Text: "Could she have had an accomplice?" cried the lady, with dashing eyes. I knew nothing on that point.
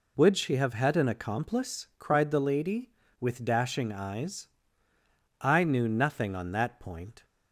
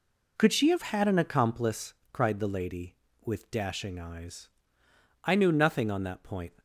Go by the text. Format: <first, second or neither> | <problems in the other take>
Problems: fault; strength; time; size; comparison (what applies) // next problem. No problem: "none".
second | says "Would" for "Could"; at 0.1 s